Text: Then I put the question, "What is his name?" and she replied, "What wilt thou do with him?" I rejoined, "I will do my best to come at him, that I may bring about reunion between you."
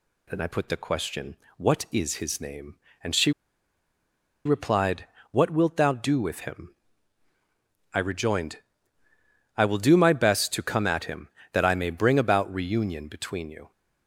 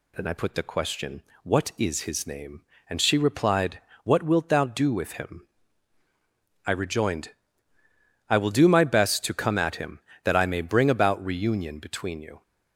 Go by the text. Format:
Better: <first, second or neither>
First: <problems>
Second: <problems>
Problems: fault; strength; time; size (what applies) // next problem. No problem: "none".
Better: second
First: pauses between "she" and "replied"; at 3.3 s; 1.1 s long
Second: none